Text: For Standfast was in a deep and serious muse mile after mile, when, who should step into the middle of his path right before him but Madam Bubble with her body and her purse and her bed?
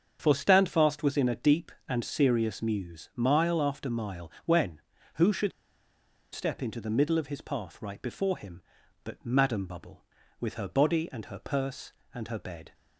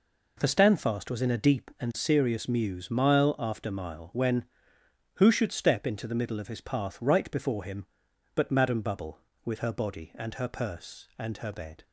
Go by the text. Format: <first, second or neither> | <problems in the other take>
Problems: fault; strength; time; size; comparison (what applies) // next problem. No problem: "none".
second | starts louder than the rest; strong; until 1.2 s; 7.5 dB // pauses between "should" and "step"; noticeable; at 5.5 s; 0.83 s long